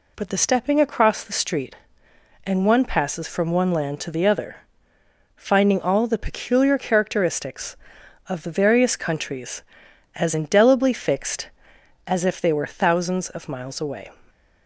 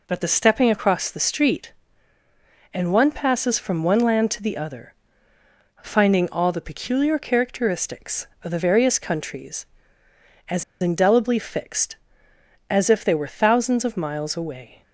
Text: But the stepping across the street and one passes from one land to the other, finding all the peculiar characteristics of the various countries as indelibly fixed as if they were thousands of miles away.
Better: first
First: none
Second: pauses between "as" and "indelibly"; slight; at 10.6 s; 0.18 s long

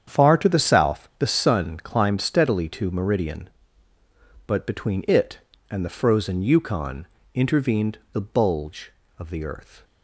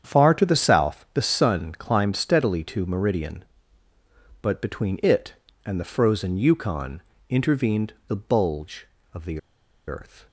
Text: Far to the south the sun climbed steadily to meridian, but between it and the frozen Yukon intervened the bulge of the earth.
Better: first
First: starts louder than the rest; strong; until 1.2 s; 8 dB // pauses between "Yukon" and "intervened"; slight; at 7.0 s; 0.30 s long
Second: starts louder than the rest; strong; until 1.1 s; 8.5 dB // pauses between "Yukon" and "intervened"; slight; at 7.0 s; 0.30 s long // pauses between "the" and "earth"; noticeable; at 9.3 s; 0.48 s long

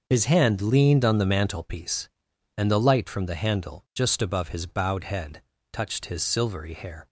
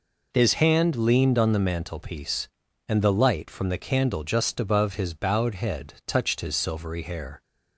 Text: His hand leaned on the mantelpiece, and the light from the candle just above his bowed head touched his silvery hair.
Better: second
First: starts louder than the rest; until 1.0 s; 6.5 dB // says "handle" for "candle"; at 3.3 s // pauses between "head" and "touched"; slight; at 5.4 s; 0.32 s long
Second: none

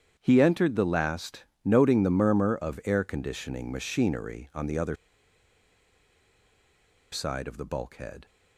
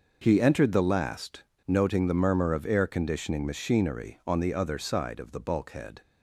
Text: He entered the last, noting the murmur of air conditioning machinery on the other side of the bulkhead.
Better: second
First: starts louder than the rest; strong; until 1.1 s; 8.5 dB // pauses between "other" and "side"; strong; at 4.9 s; 2.1 s long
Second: starts louder than the rest; noticeable; until 1.2 s; 6 dB

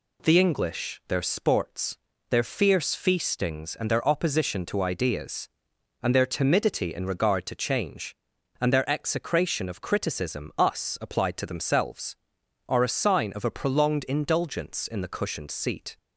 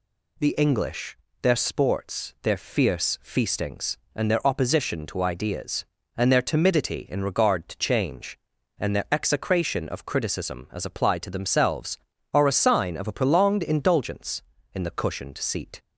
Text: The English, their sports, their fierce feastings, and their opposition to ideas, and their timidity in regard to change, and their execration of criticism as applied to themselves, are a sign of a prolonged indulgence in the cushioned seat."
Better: second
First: says "us" for "as"; at 10.5 s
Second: none

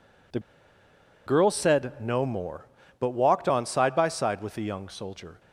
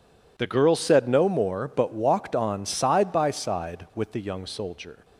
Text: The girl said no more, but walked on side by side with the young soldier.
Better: second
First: pauses between "The" and "girl"; noticeable; at 0.3 s; 0.87 s long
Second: none

